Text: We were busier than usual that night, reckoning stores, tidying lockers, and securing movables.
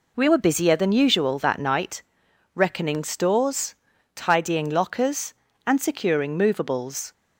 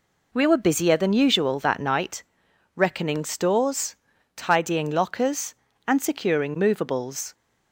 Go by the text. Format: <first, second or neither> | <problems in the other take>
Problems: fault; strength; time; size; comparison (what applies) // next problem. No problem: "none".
neither | none